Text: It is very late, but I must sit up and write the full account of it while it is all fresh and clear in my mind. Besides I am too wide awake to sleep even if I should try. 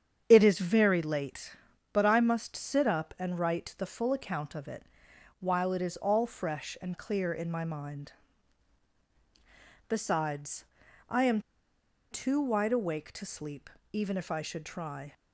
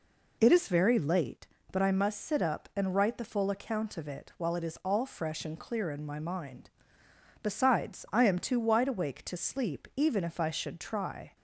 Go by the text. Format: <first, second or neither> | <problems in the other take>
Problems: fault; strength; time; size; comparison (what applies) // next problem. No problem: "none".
second | starts louder than the rest; strong; until 1.2 s; 8 dB // pauses between "it" and "while"; noticeable; at 4.8 s; 0.56 s long // pauses between "Besides" and "I"; noticeable; at 10.6 s; 0.46 s long // pauses between "am" and "too"; noticeable; at 11.4 s; 0.68 s long // pauses between "sleep" and "even"; slight; at 13.7 s; 0.20 s long